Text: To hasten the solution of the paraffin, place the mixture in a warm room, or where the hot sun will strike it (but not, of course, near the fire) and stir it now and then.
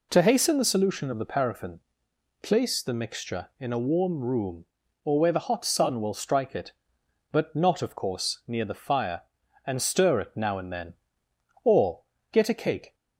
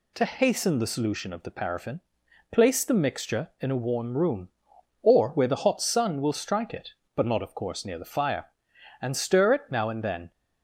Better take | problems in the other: second | goes on to say "Or get a cake"; from 11.6 s on; 1.3 s long

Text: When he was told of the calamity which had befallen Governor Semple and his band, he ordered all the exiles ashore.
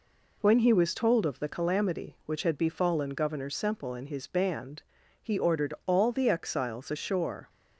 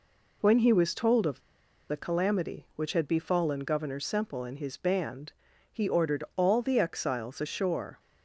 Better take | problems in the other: first | pauses between "of" and "the"; noticeable; at 1.4 s; 0.47 s long

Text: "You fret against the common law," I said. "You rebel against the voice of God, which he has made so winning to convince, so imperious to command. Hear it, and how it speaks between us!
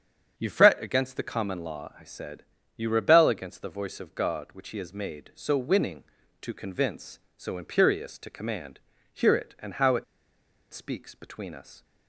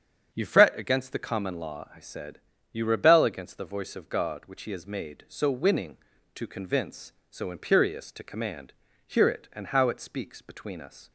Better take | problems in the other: second | starts louder than the rest; strong; until 1.3 s; 8 dB; strong in the second // pauses between "it" and "speaks"; noticeable; at 10.0 s; 0.68 s long

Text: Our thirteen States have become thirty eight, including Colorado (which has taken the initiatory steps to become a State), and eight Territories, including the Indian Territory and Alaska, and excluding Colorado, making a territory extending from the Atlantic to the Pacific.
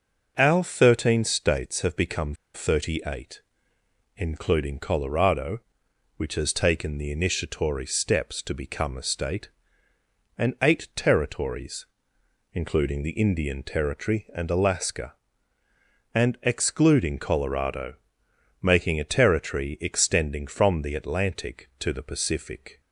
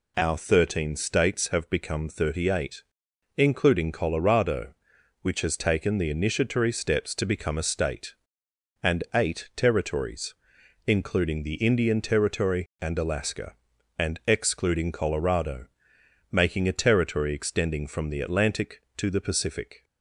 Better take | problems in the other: second | pauses between "become" and "thirty"; slight; at 2.3 s; 0.20 s long

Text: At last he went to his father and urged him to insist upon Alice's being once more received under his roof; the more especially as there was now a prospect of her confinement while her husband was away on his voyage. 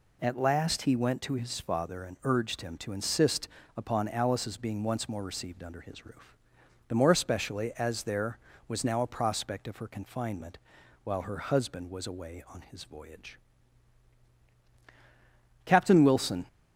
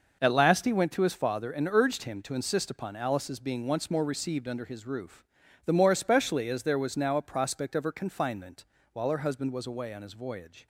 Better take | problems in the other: second | pauses between "insist" and "upon"; slight; at 3.4 s; 0.28 s long // pauses between "confinement" and "while"; noticeable; at 10.5 s; 0.46 s long; slight in the second // goes on to say "Captain Wilson"; noticeable; from 15.6 s on; 0.80 s long

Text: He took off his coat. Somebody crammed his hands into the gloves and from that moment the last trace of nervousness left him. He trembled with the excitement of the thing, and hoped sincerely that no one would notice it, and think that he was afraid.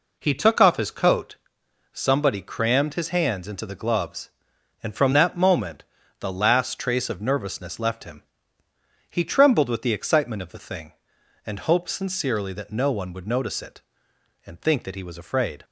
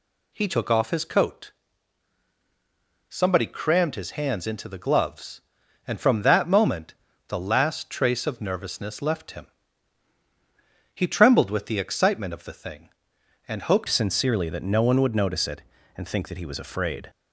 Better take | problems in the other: first | pauses between "moment" and "the"; slight; at 6.9 s; 0.32 s long; slight in the first // changes voice at "sincerely"; from 13.8 s on; 3.2 s long

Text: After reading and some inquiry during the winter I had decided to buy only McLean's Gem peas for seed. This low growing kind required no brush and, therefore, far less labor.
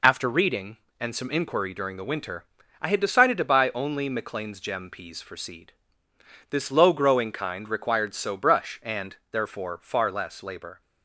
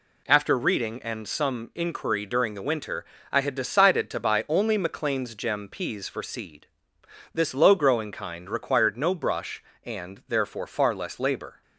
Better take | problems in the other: second | pauses between "winter" and "I"; slight; at 2.4 s; 0.36 s long; slight in the second // says "so" for "no"; at 8.1 s

